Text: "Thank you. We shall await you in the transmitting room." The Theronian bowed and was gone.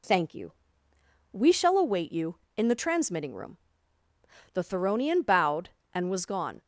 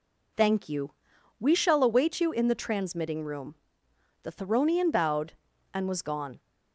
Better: neither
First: none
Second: none

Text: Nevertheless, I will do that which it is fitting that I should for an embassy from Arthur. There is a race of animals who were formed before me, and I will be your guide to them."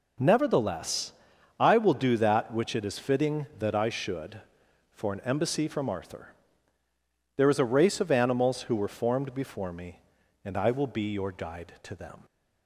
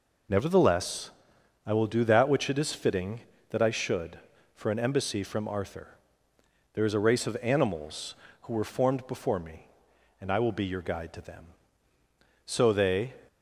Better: first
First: none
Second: goes on to say "So they"; noticeable; from 12.4 s on; 0.68 s long

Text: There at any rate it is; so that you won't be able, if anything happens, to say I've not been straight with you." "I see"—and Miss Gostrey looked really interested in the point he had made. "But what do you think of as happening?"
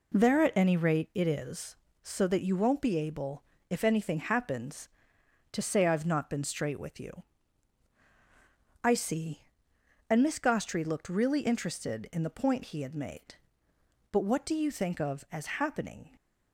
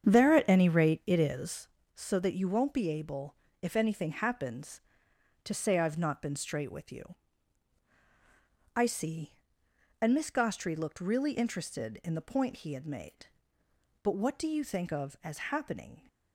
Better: first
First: none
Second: starts louder than the rest; strong; until 1.6 s; 8 dB

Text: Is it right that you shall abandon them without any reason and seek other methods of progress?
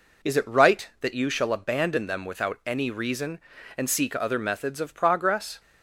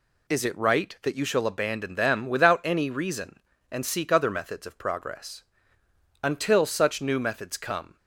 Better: first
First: none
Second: goes on to say "Until such new methods come"; strong; from 6.2 s on; 1.7 s long

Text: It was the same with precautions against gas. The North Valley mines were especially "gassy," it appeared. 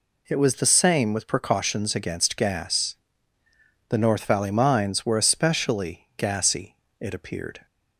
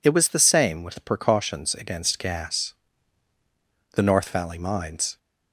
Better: first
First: none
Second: stops before "were especially gassy it appeared"; at 5.1 s

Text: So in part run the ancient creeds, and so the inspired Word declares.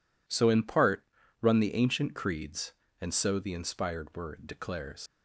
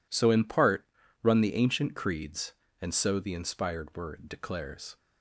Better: second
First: pauses between "part" and "run"; slight; at 1.0 s; 0.36 s long // leaves "declares" unfinished; at 5.0 s; 90 ms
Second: pauses between "part" and "run"; slight; at 0.8 s; 0.36 s long

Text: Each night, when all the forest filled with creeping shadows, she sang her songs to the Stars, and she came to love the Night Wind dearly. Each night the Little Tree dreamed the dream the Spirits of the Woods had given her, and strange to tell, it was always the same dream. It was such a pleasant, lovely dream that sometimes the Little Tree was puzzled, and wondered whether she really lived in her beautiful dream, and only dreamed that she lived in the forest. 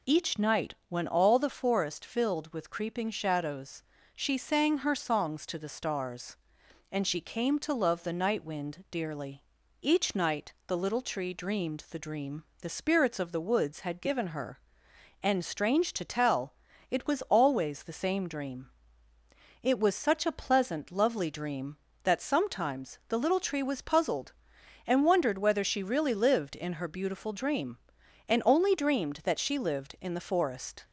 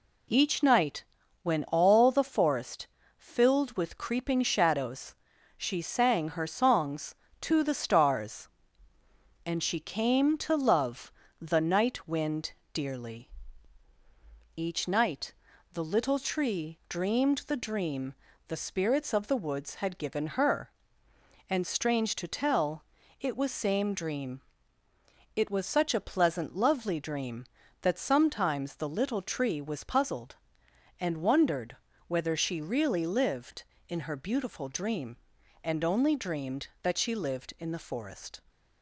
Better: first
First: pauses between "dream" and "the"; slight; at 12.4 s; 0.16 s long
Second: pauses between "forest" and "filled"; slight; at 2.8 s; 0.32 s long // pauses between "love" and "the"; slight; at 11.1 s; 0.30 s long // pauses between "Wind" and "dearly"; slight; at 12.5 s; 0.22 s long // pauses between "night" and "the"; at 15.3 s; 0.40 s long // pauses between "dream" and "the"; slight; at 18.1 s; 0.36 s long // skips "always the"; at 23.5 s // pauses between "wondered" and "whether"; slight; at 31.7 s; 0.32 s long

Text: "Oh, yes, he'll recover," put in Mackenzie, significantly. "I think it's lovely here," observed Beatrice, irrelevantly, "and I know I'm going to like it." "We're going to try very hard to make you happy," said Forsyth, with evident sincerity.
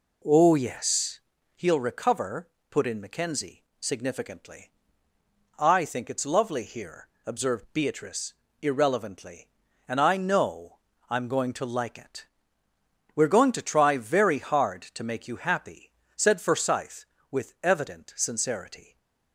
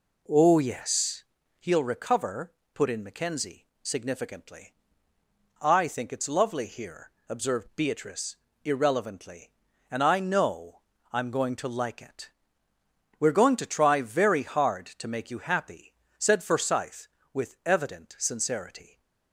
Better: neither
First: pauses between "know" and "I'm"; slight; at 10.7 s; 0.30 s long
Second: pauses between "know" and "I'm"; slight; at 10.8 s; 0.30 s long

